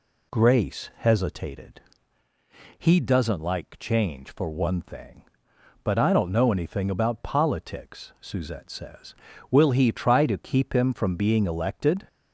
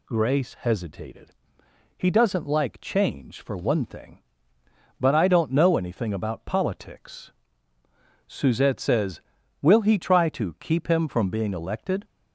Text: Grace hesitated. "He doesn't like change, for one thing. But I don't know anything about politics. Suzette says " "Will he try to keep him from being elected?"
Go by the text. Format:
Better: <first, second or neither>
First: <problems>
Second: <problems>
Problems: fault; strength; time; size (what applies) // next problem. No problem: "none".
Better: neither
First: none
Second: none